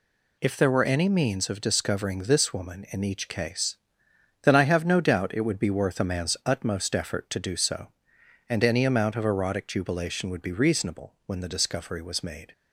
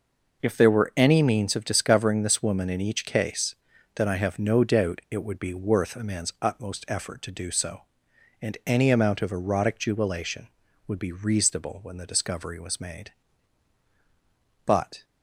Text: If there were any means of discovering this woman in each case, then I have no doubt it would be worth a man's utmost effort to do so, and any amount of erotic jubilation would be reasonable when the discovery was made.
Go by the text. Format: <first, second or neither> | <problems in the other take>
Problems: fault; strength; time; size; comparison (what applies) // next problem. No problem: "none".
first | goes on to say "But"; slight; from 14.6 s on; 0.40 s long